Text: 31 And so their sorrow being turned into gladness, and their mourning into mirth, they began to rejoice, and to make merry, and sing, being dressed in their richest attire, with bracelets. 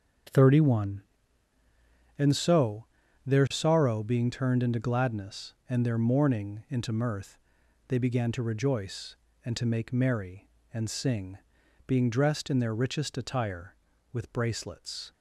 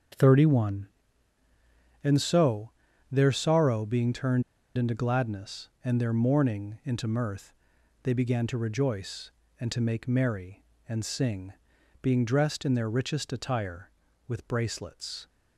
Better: first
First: starts louder than the rest; until 2.4 s; 6.5 dB // pauses between "so" and "their"; at 2.8 s; 0.42 s long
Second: starts louder than the rest; until 2.2 s; 6.5 dB // pauses between "so" and "their"; at 2.6 s; 0.42 s long // pauses between "turned" and "into"; slight; at 4.4 s; 0.34 s long

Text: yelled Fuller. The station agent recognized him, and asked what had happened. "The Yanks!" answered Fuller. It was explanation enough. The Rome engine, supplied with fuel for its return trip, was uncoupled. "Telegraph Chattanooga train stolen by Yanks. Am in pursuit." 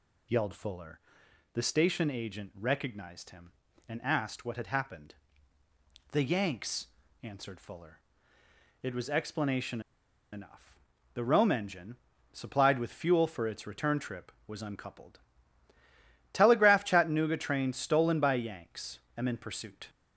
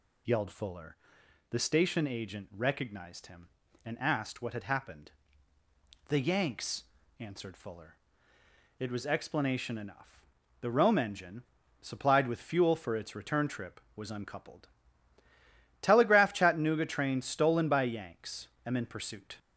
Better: second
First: pauses between "explanation" and "enough"; noticeable; at 9.8 s; 0.51 s long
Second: none

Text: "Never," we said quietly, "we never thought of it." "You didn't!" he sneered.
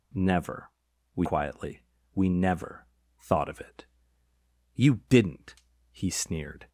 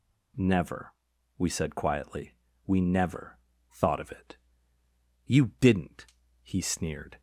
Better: second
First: skips "said"; at 1.2 s // pauses between "never" and "thought"; slight; at 2.8 s; 0.34 s long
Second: pauses between "never" and "thought"; slight; at 3.3 s; 0.34 s long

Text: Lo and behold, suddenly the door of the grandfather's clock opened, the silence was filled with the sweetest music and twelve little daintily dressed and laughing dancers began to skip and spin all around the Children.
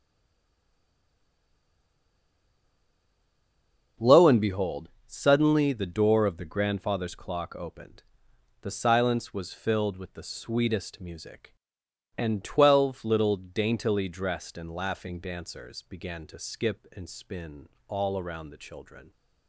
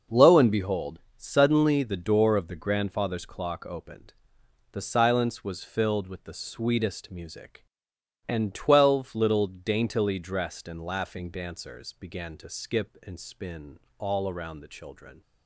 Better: second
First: stays silent before the first word; strong; until 3.9 s; 3.9 s long // pauses between "spin" and "all"; slight; at 17.6 s; 0.18 s long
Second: pauses between "spin" and "all"; slight; at 13.7 s; 0.18 s long

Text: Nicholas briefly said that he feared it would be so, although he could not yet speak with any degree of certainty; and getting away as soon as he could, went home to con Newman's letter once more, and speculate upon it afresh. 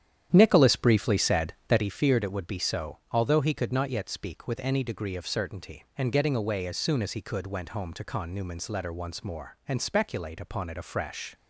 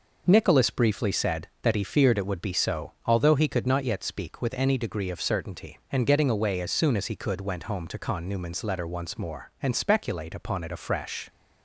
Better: second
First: starts louder than the rest; strong; until 1.8 s; 10 dB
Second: none

